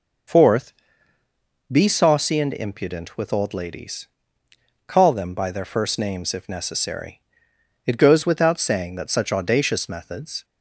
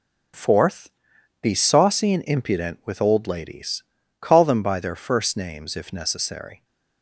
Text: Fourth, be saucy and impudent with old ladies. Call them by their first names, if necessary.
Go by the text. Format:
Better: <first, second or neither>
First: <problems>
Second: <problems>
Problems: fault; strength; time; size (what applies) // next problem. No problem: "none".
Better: second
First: goes on to say "It goes without saying that such audacious methods"; strong; from 7.8 s on; 2.5 s long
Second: none